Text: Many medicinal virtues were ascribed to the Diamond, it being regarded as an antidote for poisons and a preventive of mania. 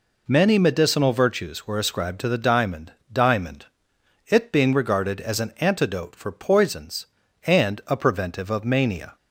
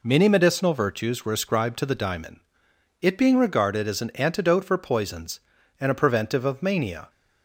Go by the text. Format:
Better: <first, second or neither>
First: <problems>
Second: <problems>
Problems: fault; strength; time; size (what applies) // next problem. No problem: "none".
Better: second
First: says "Diamond" twice; at 3.1 s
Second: none